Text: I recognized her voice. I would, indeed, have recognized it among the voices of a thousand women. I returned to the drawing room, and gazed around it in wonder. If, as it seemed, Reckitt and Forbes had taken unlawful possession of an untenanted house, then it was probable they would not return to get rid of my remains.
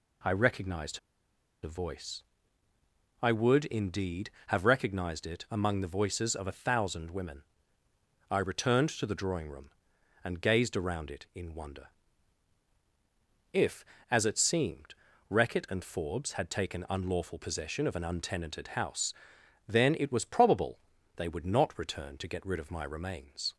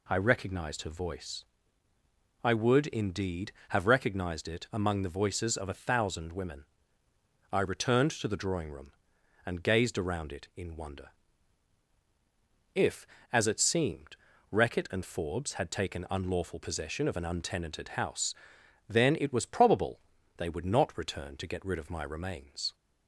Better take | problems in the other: second | pauses between "recognized" and "her"; noticeable; at 0.9 s; 0.64 s long // pauses between "probable" and "they"; at 20.7 s; 0.38 s long; also in the second

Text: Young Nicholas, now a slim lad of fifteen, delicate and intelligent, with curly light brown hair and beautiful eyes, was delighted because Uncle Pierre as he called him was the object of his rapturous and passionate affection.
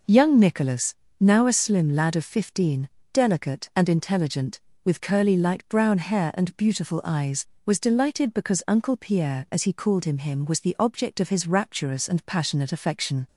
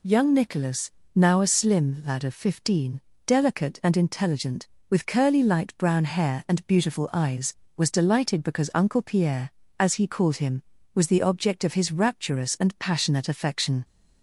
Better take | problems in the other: second | says "him" twice; at 10.1 s

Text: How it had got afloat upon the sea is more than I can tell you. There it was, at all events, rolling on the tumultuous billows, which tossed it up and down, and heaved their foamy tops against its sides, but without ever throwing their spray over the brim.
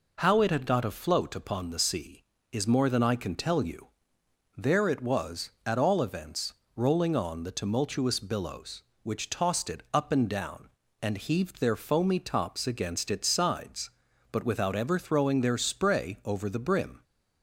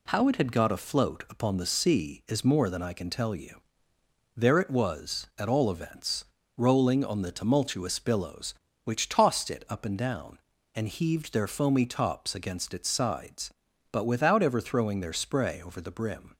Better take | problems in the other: neither | none

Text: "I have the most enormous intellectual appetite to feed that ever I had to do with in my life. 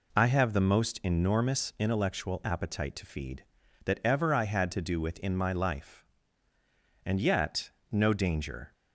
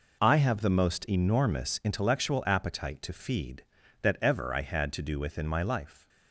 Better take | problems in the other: second | goes on to say "And yet no danger"; strong; from 7.0 s on; 1.6 s long

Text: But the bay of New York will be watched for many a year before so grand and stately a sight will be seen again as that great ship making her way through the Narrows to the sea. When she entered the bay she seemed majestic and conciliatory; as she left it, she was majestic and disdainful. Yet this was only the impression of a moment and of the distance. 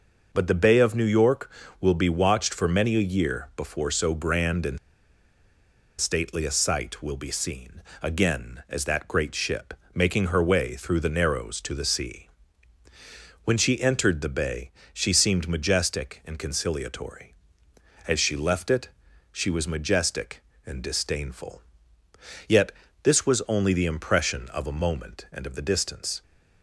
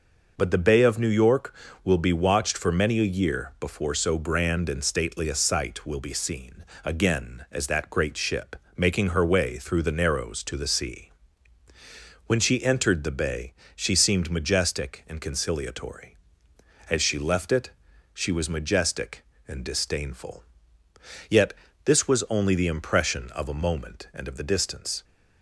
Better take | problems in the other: second | pauses between "and" and "stately"; at 4.7 s; 1.2 s long // pauses between "seen" and "again"; slight; at 7.8 s; 0.20 s long; slight in the second // pauses between "ship" and "making"; slight; at 9.7 s; 0.20 s long; slight in the second // pauses between "bay" and "she"; slight; at 14.6 s; 0.24 s long; slight in the second // pauses between "Yet" and "this"; slight; at 22.7 s; 0.30 s long; slight in the second

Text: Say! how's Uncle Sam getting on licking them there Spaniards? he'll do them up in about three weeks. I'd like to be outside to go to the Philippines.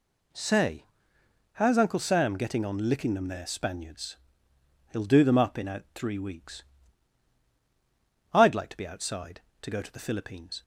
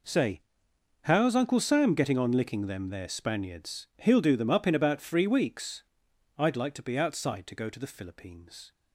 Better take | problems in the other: second | says "out" for "about"; at 5.6 s

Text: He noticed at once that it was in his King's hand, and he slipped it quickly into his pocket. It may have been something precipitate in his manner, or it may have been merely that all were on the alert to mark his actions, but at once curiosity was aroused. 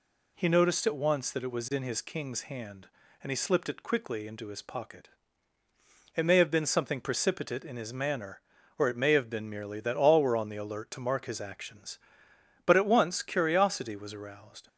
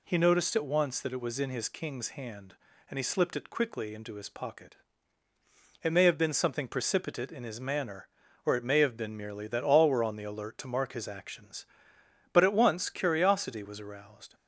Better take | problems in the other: neither | none

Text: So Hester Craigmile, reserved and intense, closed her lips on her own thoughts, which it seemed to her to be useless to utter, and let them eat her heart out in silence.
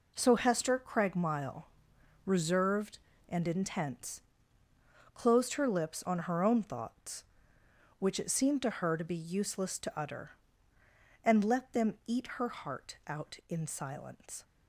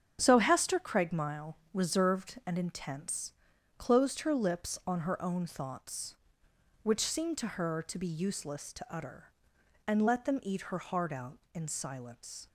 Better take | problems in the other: first | starts louder than the rest; strong; until 1.2 s; 7.5 dB // skips "it"; at 6.9 s

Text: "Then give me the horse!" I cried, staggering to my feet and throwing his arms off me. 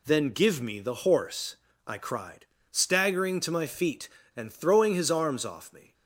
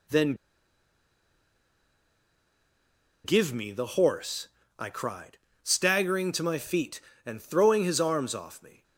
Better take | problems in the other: first | pauses between "Then" and "give"; strong; at 0.3 s; 2.8 s long

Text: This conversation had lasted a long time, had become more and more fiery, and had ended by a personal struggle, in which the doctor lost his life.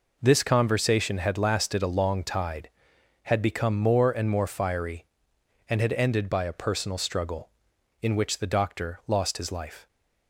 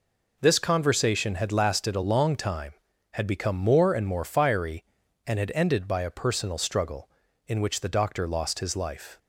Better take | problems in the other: second | says "tide" for "time"; at 2.2 s

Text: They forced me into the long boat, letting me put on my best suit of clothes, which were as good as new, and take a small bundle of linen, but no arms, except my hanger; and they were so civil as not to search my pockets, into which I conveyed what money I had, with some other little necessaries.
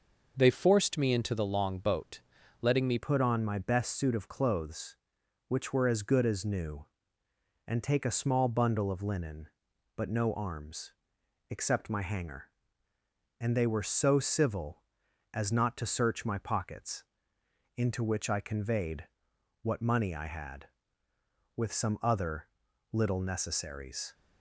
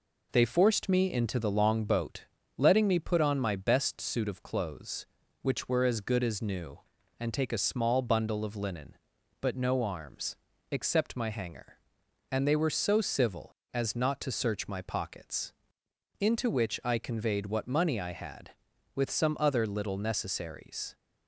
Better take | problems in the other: second | changes voice at "put"; from 2.9 s on; 21.2 s long // pauses between "conveyed" and "what"; noticeable; at 19.0 s; 0.56 s long // pauses between "other" and "little"; noticeable; at 22.4 s; 0.46 s long

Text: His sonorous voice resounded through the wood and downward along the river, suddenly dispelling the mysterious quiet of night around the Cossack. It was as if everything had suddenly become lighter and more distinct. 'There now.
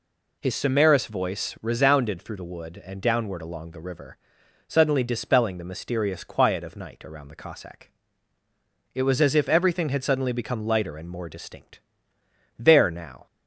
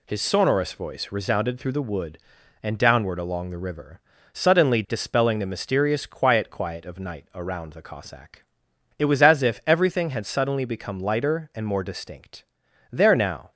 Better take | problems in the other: first | says "quiet" twice; at 6.4 s

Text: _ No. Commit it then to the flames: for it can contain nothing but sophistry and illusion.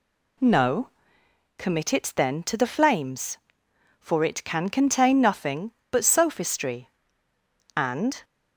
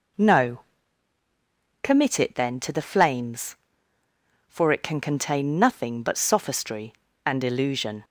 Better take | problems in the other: second | stops before "illusion"; at 8.2 s

